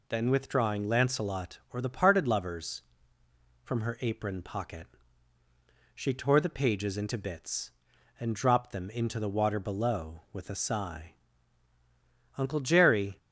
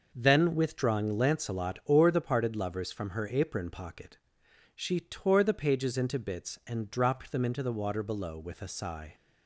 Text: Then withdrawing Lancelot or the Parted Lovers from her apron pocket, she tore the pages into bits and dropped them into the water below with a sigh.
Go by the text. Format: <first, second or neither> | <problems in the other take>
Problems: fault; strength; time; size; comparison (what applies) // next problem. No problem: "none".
second | goes on to say "Uncle Jerry"; noticeable; from 12.3 s on; 0.80 s long